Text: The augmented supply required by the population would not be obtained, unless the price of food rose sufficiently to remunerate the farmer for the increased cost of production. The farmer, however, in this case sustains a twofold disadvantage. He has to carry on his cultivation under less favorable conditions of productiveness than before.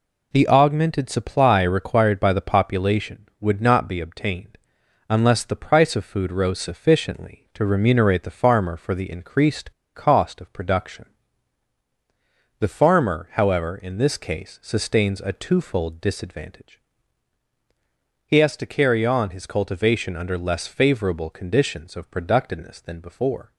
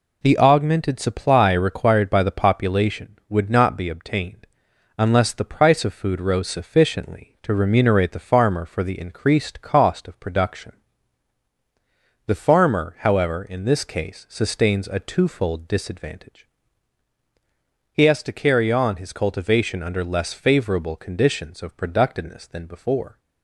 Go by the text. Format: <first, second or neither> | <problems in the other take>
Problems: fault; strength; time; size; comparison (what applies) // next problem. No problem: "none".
second | pauses between "increased" and "cost"; slight; at 9.7 s; 0.22 s long